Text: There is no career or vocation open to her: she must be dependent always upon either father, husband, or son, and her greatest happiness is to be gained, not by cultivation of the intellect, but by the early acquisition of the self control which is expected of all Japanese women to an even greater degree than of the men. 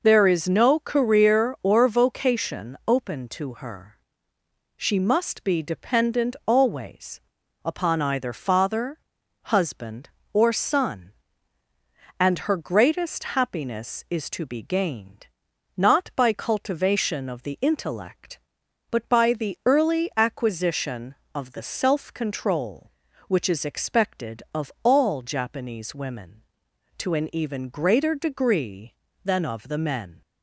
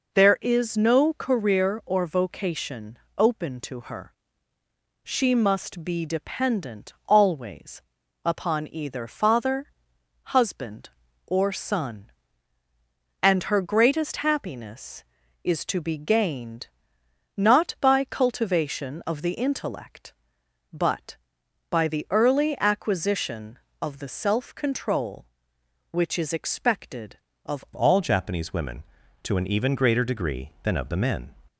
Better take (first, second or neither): first